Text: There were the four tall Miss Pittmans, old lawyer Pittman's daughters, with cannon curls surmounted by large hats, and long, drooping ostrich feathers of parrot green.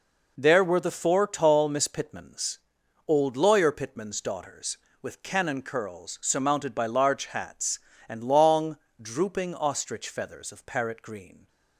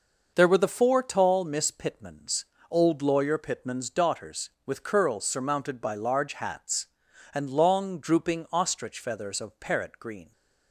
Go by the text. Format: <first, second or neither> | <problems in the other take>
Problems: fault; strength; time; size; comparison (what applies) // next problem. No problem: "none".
first | skips "cannon"; at 4.8 s